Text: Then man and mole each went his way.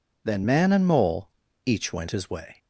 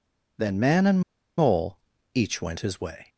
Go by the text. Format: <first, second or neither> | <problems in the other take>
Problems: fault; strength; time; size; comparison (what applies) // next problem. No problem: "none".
first | pauses between "and" and "mole"; at 1.0 s; 0.37 s long // pauses between "mole" and "each"; slight; at 1.7 s; 0.36 s long; slight in the first